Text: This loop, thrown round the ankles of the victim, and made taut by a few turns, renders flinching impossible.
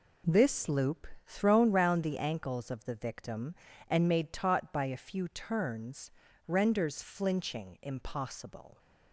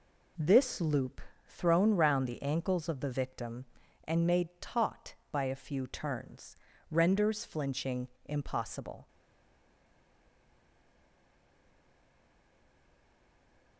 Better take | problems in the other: first | pauses between "flinching" and "impossible"; slight; at 8.0 s; 0.18 s long // stays silent after the last word; strong; from 9.0 s on; 4.7 s long

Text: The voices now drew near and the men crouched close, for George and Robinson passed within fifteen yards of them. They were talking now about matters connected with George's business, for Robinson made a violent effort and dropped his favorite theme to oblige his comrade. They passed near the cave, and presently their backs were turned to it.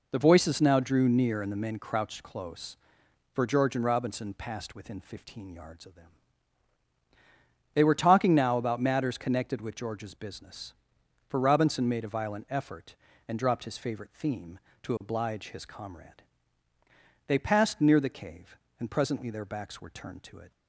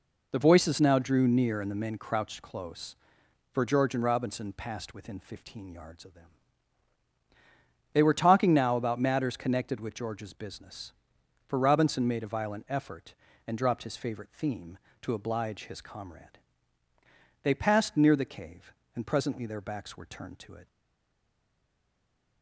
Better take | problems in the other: first | stays silent after the last word; noticeable; from 20.6 s on; 1.8 s long

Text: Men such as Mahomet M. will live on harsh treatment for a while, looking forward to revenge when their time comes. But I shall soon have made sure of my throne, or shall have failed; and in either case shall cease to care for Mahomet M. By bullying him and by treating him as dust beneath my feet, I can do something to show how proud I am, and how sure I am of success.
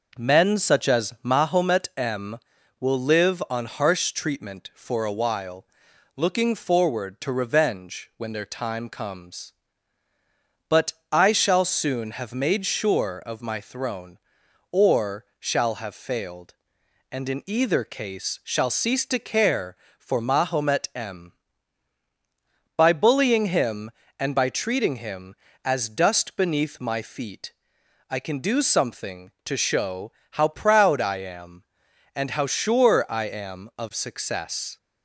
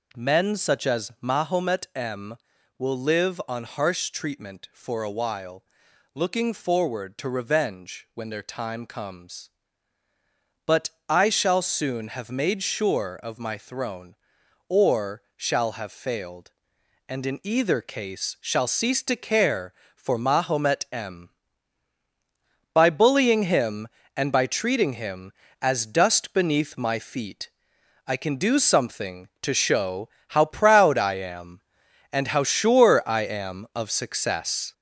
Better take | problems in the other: first | gets louder; noticeable; throughout; 4.5 dB // pauses between "But" and "I"; slight; at 10.8 s; 0.20 s long; slight in the first // pauses between "or" and "shall"; slight; at 15.2 s; 0.16 s long; slight in the first // pauses between "show" and "how"; slight; at 30.0 s; 0.20 s long; slight in the first

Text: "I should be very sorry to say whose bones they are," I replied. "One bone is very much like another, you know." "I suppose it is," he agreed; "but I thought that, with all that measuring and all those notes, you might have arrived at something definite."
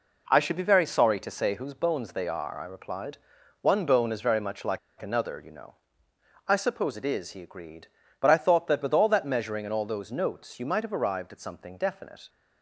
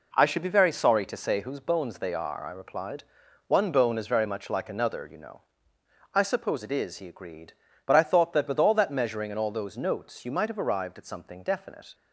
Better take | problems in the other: second | pauses between "like" and "another"; slight; at 4.7 s; 0.21 s long

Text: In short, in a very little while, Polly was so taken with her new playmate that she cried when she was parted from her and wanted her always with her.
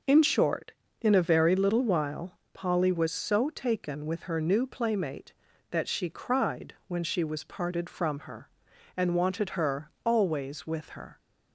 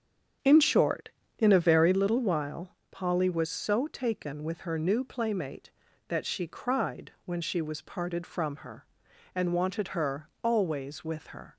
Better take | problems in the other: first | starts louder than the rest; strong; until 2.1 s; 8 dB

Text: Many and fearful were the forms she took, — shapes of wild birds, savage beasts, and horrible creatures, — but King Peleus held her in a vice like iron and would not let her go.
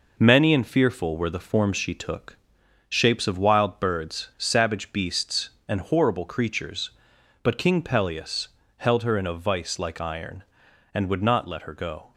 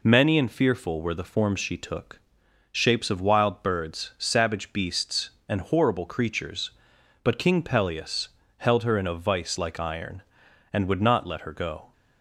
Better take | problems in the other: second | gets quieter; noticeable; throughout; 5 dB // pauses between "Peleus" and "held"; slight; at 8.4 s; 0.30 s long; slight in the second

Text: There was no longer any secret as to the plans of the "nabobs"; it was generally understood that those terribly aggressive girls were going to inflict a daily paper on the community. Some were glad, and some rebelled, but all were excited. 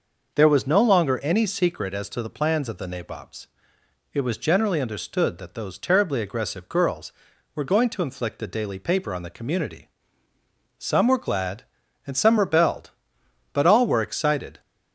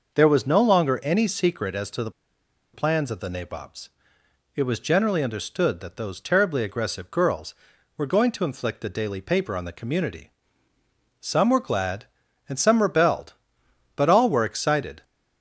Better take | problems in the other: first | pauses between "the" and "plans"; noticeable; at 2.0 s; 0.63 s long

